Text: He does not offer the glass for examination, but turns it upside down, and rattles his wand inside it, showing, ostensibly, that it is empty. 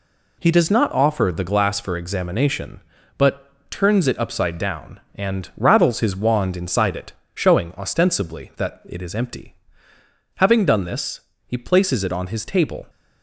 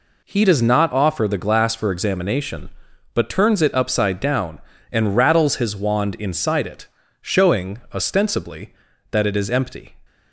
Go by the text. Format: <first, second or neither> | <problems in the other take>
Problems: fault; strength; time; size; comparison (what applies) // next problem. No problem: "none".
second | pauses between "but" and "turns"; slight; at 3.5 s; 0.18 s long // goes on to say "Having done this he places it on his table"; strong; from 10.3 s on; 2.5 s long